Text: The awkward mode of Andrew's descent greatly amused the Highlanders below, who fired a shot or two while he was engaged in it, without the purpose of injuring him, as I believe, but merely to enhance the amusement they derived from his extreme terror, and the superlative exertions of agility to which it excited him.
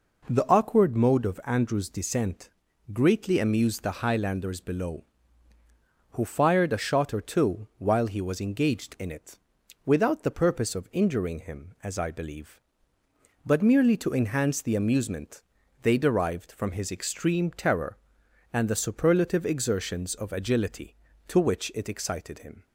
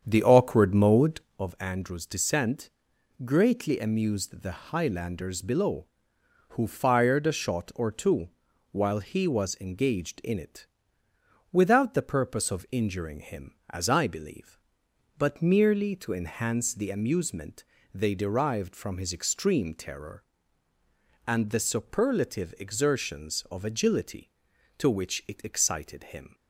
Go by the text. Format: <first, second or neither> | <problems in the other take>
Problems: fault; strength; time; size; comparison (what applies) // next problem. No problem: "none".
first | starts louder than the rest; strong; until 1.4 s; 8 dB // pauses between "descent" and "greatly"; noticeable; at 2.7 s; 0.54 s long; noticeable in the first // pauses between "two" and "while"; at 8.2 s; 0.44 s long // pauses between "amusement" and "they"; slight; at 17.6 s; 0.32 s long; also in the first